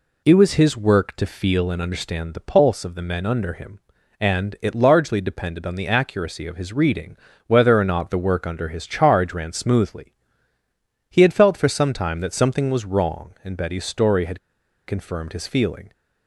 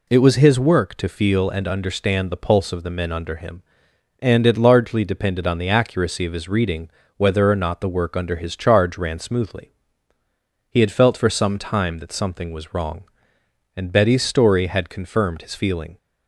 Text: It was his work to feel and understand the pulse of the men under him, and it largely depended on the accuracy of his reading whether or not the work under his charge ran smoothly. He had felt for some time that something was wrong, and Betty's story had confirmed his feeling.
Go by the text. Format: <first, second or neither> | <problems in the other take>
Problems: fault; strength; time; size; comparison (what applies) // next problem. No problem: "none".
second | pauses between "reading" and "whether"; slight; at 7.1 s; 0.30 s long; slight in the second // pauses between "had" and "confirmed"; noticeable; at 14.3 s; 0.47 s long